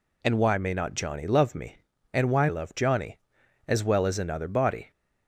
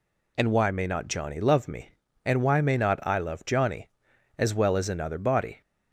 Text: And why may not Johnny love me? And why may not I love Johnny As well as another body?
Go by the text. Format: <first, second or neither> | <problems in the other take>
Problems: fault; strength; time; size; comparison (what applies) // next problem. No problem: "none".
second | skips "may not I"; at 2.4 s